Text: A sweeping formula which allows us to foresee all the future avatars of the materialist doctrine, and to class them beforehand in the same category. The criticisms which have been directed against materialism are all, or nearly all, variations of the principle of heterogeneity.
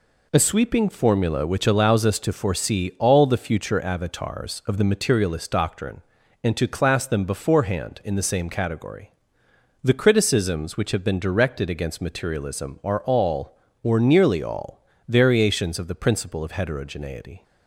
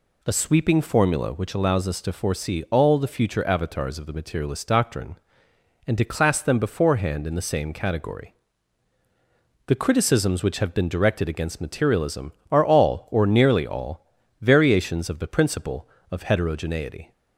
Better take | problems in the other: neither | none

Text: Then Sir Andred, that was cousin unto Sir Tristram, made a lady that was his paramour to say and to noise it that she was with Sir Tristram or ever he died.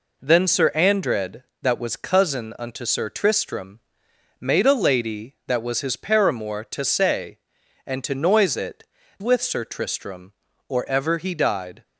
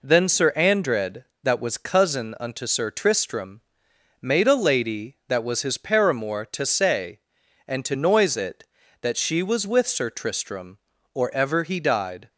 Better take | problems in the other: second | skips "that she was"; at 9.0 s

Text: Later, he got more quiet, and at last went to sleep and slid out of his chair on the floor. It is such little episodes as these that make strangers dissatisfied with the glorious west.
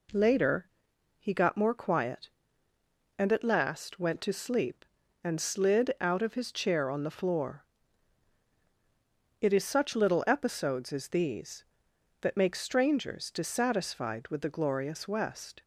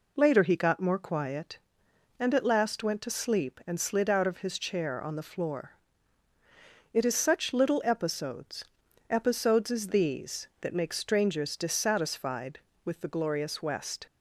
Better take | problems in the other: first | says "episodes" twice; at 9.0 s

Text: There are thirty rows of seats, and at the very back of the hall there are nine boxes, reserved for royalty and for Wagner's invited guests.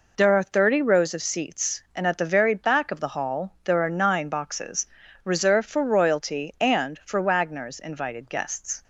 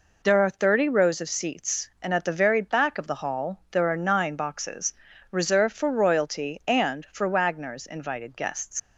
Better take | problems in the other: first | leaves "guests" unfinished; at 8.7 s; 100 ms

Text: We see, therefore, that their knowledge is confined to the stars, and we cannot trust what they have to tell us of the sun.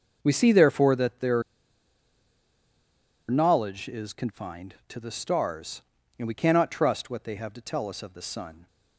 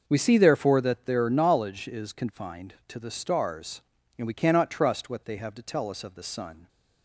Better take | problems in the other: second | pauses between "their" and "knowledge"; strong; at 1.4 s; 1.8 s long

